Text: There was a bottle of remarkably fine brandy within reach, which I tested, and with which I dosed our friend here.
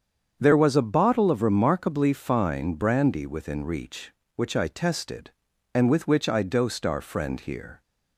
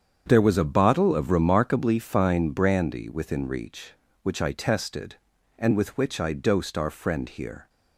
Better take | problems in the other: neither | starts louder than the rest; strong; the same in both

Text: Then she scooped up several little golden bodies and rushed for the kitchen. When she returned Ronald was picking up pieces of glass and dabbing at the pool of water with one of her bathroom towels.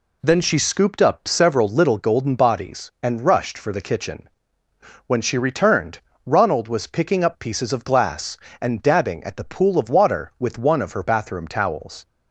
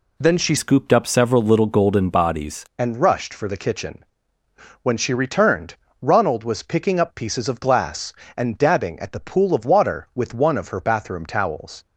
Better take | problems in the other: first | changes voice from "scooped" to "bodies"; from 0.5 to 2.6 s; 2.1 s long // pauses between "returned" and "Ronald"; slight; at 5.7 s; 0.26 s long; slight in the first

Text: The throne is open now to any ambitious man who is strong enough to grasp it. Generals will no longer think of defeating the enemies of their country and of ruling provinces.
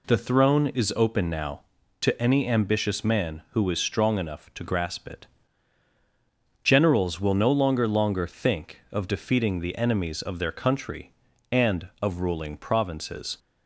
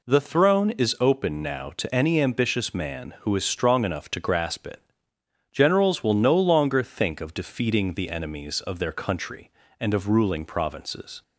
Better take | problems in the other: second | says "longer" twice; at 7.8 s

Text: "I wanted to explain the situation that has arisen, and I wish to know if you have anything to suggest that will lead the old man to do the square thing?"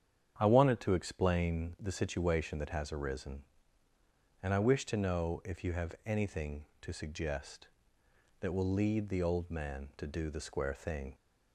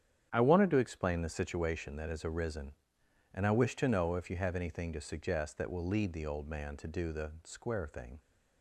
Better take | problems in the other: neither | starts louder than the rest; strong; the same in both

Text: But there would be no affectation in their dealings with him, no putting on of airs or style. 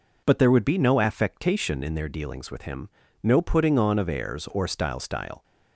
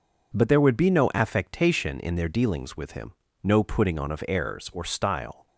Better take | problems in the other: second | says "style" twice; at 4.9 s

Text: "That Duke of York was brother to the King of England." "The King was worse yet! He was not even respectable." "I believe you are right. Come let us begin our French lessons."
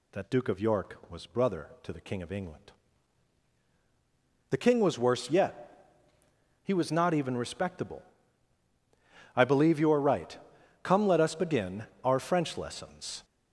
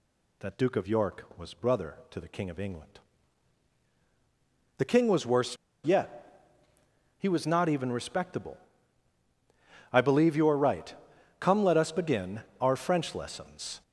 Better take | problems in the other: first | pauses between "worse" and "yet"; slight; at 5.5 s; 0.27 s long // pauses between "begin" and "our"; slight; at 12.4 s; 0.18 s long; slight in the first

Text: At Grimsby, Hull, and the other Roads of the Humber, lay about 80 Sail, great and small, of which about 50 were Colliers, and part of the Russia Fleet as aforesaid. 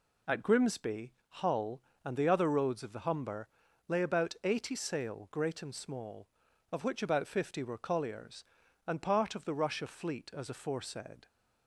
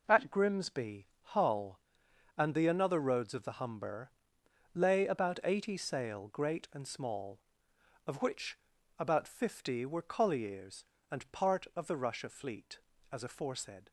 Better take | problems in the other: first | says "another" for "other"; at 2.6 s // pauses between "which" and "about"; at 8.5 s; 0.40 s long

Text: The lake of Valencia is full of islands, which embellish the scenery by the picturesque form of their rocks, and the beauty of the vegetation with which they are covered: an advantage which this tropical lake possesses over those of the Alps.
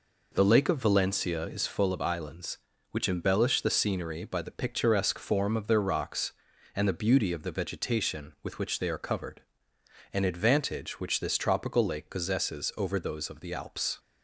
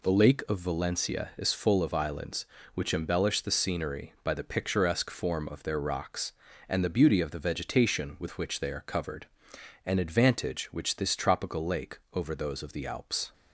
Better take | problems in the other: first | skips "possesses"; at 12.0 s

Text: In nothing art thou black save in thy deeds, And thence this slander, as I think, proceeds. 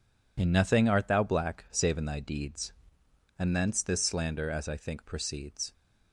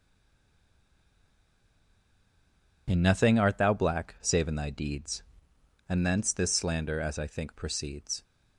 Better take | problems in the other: first | stays silent before the first word; strong; until 2.8 s; 2.8 s long

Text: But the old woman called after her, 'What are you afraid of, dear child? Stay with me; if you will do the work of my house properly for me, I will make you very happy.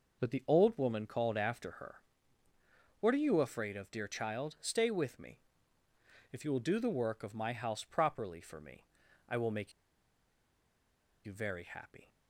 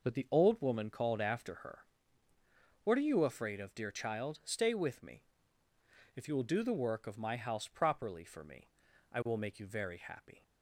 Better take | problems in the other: second | pauses between "make" and "you"; strong; at 9.7 s; 1.5 s long

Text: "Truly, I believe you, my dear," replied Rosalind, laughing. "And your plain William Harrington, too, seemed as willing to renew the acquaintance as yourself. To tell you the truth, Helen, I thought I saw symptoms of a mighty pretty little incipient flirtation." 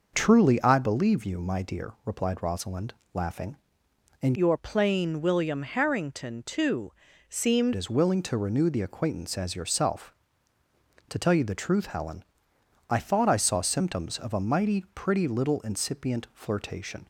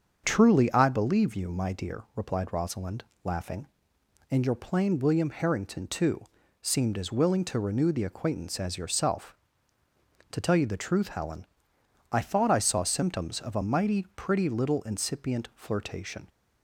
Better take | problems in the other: second | starts louder than the rest; noticeable; until 1.1 s; 6 dB; also in the second // changes voice from "your" to "seemed"; from 4.3 to 7.7 s; 3.4 s long

